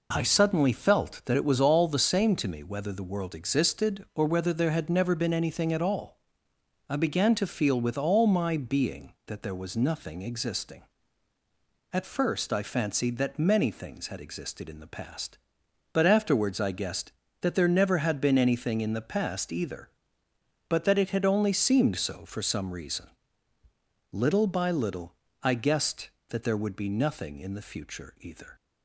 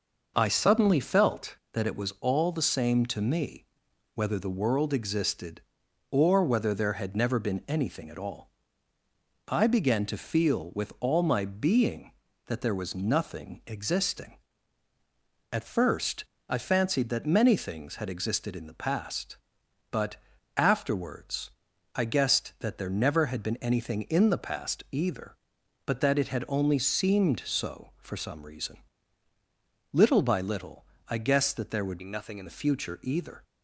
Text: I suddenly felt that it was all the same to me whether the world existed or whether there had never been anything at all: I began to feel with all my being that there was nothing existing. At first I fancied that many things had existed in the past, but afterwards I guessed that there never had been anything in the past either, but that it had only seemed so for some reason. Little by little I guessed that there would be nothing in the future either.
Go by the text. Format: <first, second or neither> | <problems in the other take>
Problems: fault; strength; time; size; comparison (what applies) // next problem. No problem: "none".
first | pauses between "me" and "whether"; noticeable; at 3.6 s; 0.48 s long // pauses between "first" and "I"; slight; at 16.2 s; 0.24 s long // pauses between "but" and "afterwards"; at 20.1 s; 0.40 s long // pauses between "afterwards" and "I"; at 21.4 s; 0.44 s long // pauses between "little" and "I"; slight; at 30.8 s; 0.24 s long; slight in the first // changes voice from "be" to "in"; from 31.9 to 32.4 s; 0.5 s long